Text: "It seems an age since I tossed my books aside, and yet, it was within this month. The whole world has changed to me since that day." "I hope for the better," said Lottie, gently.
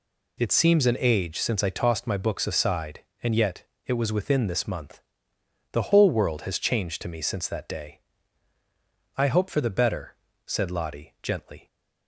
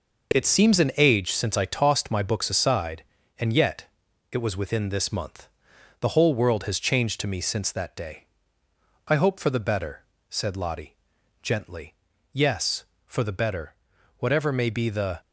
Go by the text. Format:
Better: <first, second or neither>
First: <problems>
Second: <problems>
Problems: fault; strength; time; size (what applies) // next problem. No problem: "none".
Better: first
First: none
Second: goes on to say "Yes for the better whatever may be the"; strong; from 12.3 s on; 2.8 s long